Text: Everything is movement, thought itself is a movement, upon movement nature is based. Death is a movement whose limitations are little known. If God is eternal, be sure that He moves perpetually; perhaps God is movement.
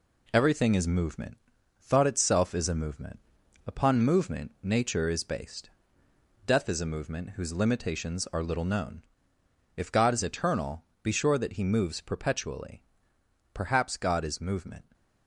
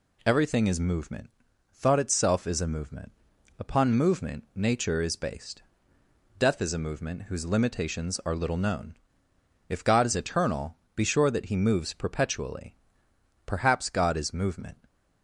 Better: second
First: gets quieter; throughout; 4 dB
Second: none

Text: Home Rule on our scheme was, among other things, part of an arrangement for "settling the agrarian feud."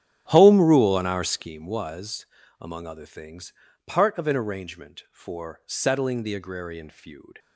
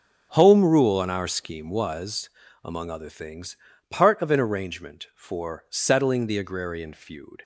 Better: second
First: starts louder than the rest; strong; until 1.5 s; 9.5 dB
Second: none

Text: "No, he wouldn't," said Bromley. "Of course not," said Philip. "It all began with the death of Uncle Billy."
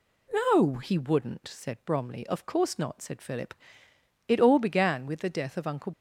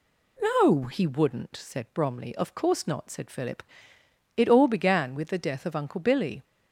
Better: second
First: stops before "Billy"; at 5.9 s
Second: none

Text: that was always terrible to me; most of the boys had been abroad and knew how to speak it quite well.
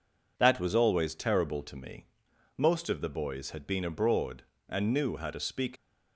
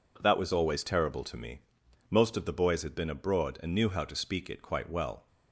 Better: second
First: stops before "it quite well"; at 5.7 s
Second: none

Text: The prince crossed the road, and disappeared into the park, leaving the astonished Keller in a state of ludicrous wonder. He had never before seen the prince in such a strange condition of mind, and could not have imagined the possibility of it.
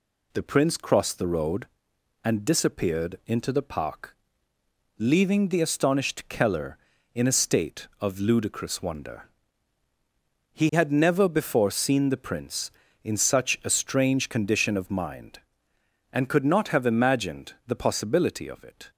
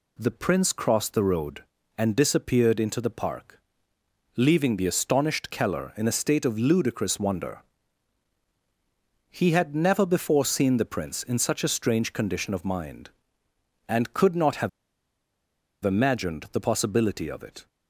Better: first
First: none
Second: pauses between "have" and "imagined"; at 14.6 s; 1.1 s long

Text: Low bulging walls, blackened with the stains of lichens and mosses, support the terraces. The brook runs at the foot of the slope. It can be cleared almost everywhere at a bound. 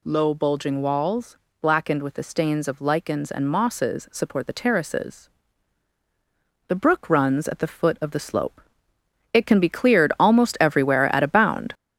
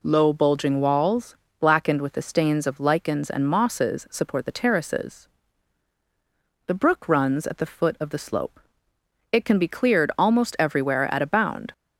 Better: second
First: gets louder; noticeable; throughout; 5.5 dB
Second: none

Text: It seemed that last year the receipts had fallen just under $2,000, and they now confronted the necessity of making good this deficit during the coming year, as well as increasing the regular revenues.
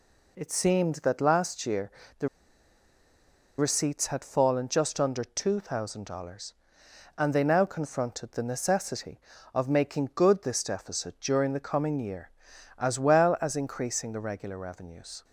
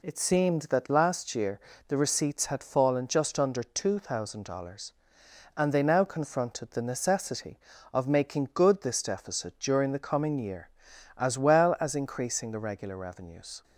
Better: second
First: pauses between "year" and "the"; slight; at 1.8 s; 0.28 s long // pauses between "the" and "receipts"; strong; at 2.2 s; 1.3 s long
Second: pauses between "year" and "the"; slight; at 1.5 s; 0.28 s long

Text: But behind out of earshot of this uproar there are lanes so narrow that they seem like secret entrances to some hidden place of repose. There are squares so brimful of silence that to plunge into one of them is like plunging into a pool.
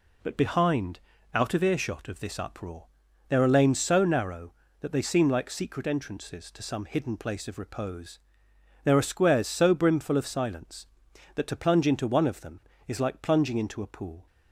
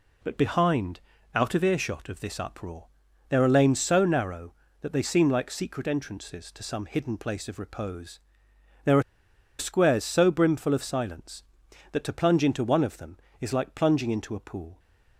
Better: first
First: pauses between "behind" and "out"; slight; at 1.0 s; 0.32 s long // pauses between "uproar" and "there"; at 2.8 s; 0.42 s long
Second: pauses between "behind" and "out"; slight; at 1.0 s; 0.32 s long // pauses between "uproar" and "there"; at 2.8 s; 0.42 s long // pauses between "are" and "squares"; noticeable; at 9.0 s; 0.56 s long

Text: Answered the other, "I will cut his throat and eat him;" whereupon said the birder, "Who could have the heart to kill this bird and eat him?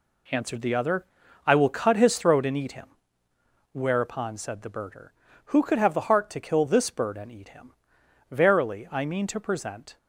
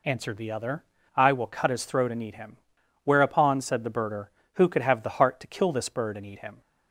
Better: second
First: goes on to say "Verily I mean to present"; from 8.3 s on; 1.6 s long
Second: none

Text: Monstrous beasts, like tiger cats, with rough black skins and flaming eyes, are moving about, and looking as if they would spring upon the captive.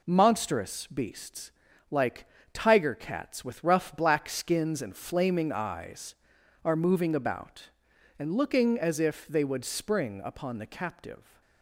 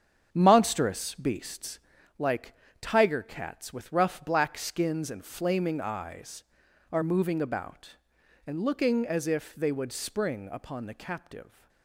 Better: first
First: pauses between "like" and "tiger"; slight; at 2.2 s; 0.28 s long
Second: starts louder than the rest; strong; until 2.1 s; 8 dB // pauses between "like" and "tiger"; slight; at 2.5 s; 0.28 s long

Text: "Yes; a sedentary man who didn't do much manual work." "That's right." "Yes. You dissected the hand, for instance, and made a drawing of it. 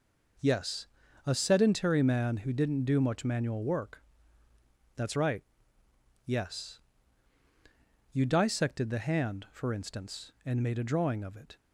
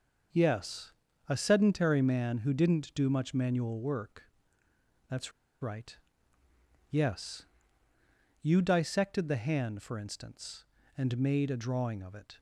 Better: first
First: none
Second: starts louder than the rest; until 1.6 s; 6 dB // pauses between "That's" and "right"; slight; at 5.3 s; 0.30 s long

